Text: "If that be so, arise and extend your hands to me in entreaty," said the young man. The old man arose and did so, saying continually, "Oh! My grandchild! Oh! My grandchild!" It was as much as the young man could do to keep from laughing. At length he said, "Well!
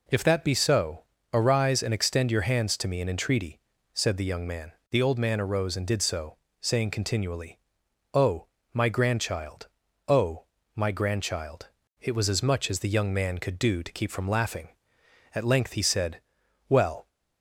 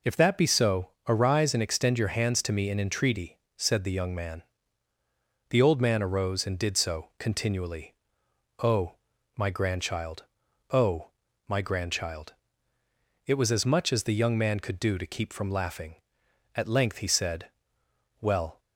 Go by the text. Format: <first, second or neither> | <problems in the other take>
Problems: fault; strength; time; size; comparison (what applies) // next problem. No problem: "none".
first | skips "saying"; at 7.1 s